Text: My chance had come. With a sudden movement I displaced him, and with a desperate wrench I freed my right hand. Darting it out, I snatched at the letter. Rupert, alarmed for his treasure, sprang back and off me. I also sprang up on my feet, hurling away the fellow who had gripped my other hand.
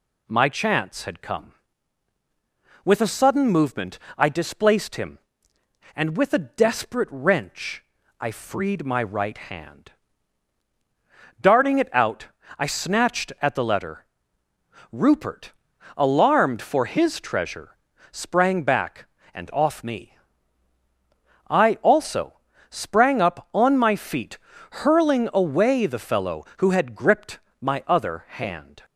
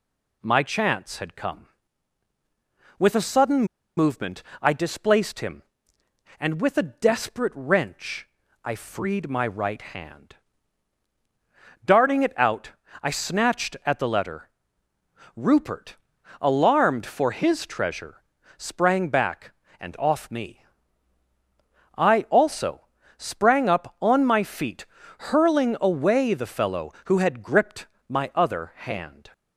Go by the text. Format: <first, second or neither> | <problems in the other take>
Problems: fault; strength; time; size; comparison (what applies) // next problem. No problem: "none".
first | pauses between "sudden" and "movement"; slight; at 3.6 s; 0.32 s long // pauses between "movement" and "I"; slight; at 4.4 s; 0.18 s long; slight in the first // pauses between "wrench" and "I"; slight; at 8.2 s; 0.36 s long; slight in the first // pauses between "also" and "sprang"; slight; at 22.8 s; 0.36 s long; slight in the first // pauses between "gripped" and "my"; slight; at 27.8 s; 0.20 s long; slight in the first